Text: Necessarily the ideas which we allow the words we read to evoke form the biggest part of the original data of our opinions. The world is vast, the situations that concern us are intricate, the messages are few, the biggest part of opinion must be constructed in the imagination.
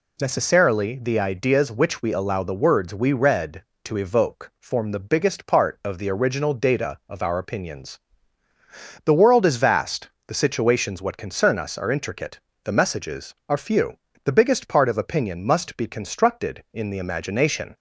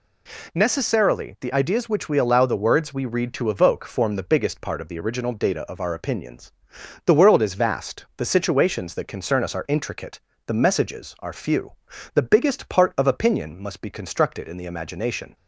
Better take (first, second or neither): second